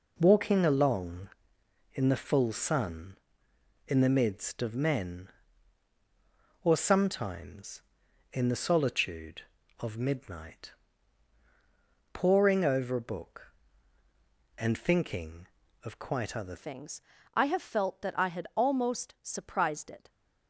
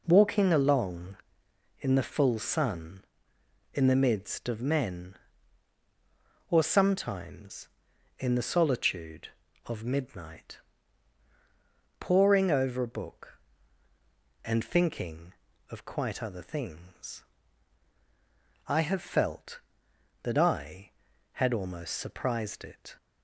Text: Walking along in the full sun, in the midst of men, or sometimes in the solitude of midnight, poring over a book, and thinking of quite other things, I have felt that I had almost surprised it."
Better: second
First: changes voice at "things"; from 16.5 s on; 3.5 s long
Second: none

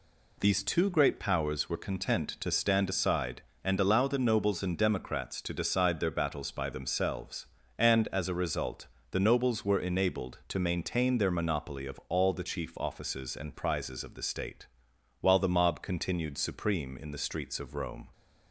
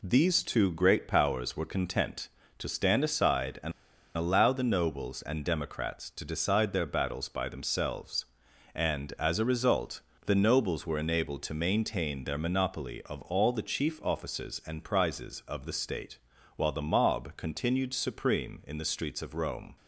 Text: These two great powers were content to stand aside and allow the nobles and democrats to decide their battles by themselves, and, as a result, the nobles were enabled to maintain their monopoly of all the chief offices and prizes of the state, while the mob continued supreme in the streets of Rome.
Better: first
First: none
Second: pauses between "and" and "allow"; noticeable; at 3.7 s; 0.45 s long

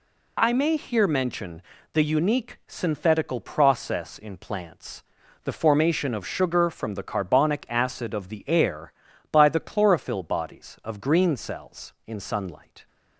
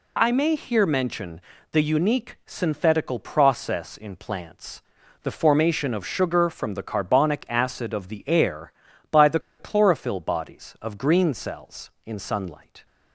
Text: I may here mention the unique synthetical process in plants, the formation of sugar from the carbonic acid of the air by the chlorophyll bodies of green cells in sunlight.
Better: first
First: pauses between "mention" and "the"; slight; at 1.6 s; 0.32 s long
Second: pauses between "mention" and "the"; slight; at 1.4 s; 0.32 s long // pauses between "the" and "chlorophyll"; slight; at 9.3 s; 0.20 s long

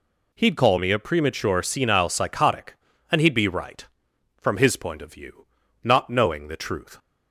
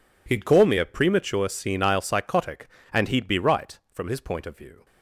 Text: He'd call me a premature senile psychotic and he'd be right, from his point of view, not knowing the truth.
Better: first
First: none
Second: stops before "not knowing the truth"; at 4.8 s

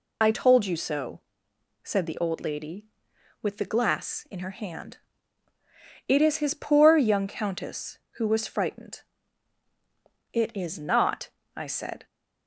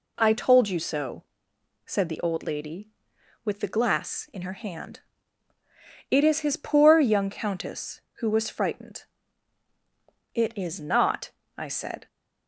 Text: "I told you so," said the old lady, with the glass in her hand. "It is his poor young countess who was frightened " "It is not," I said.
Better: second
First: loses the start of "I"; at 0.2 s; 55 ms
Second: none

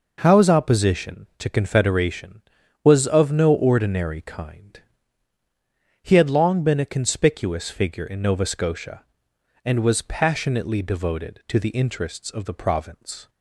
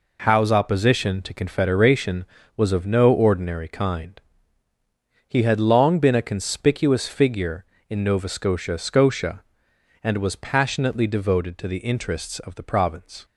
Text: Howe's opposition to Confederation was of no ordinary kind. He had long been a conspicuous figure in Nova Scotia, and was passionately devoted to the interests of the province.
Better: first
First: none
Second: says "Scotia" twice; at 8.7 s

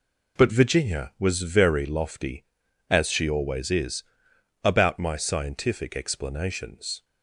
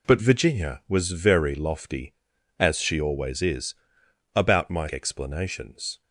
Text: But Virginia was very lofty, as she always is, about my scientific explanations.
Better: first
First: none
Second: skips "scientific"; at 4.8 s

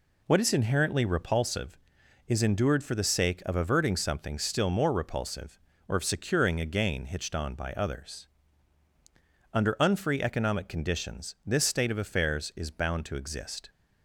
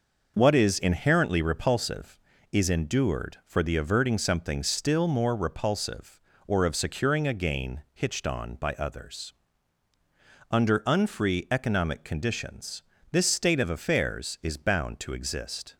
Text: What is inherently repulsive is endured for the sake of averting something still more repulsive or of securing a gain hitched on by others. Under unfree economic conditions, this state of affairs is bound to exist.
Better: first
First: none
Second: skips "sake of"; at 3.7 s

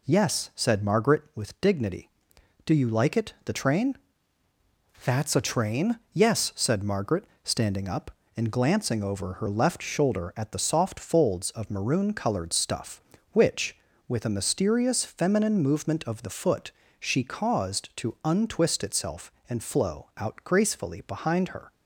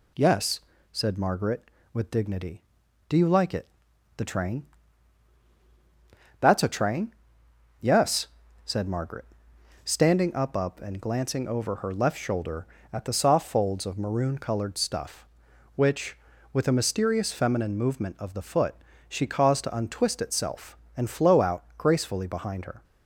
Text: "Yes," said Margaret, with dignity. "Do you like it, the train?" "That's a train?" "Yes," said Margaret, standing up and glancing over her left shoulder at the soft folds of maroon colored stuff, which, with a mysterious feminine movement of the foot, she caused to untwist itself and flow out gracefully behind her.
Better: first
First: none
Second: says "up" twice; at 10.5 s

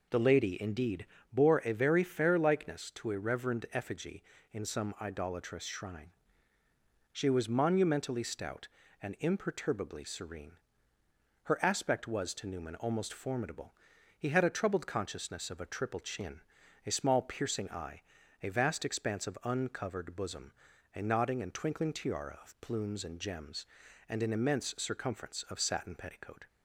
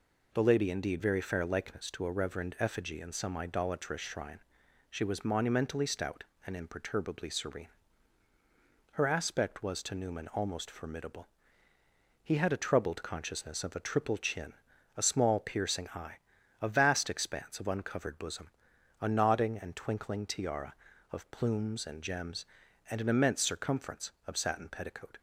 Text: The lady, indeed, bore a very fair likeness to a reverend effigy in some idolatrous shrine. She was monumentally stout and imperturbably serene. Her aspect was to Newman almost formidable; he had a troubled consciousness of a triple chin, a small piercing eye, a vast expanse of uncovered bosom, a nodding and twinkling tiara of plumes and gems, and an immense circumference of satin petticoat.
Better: first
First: none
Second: skips "bore a"; at 1.0 s

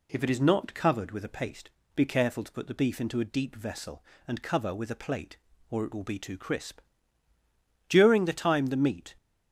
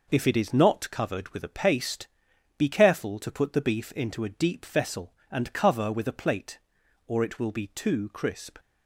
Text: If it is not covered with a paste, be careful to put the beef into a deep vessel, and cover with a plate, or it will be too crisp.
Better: second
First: goes on to say "During the time the meat"; noticeable; from 7.8 s on; 1.2 s long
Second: none

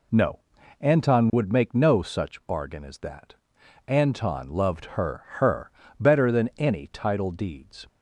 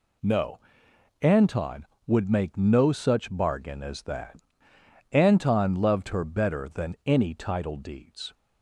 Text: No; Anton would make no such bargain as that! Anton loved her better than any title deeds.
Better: second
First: says "her" twice; at 5.3 s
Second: none

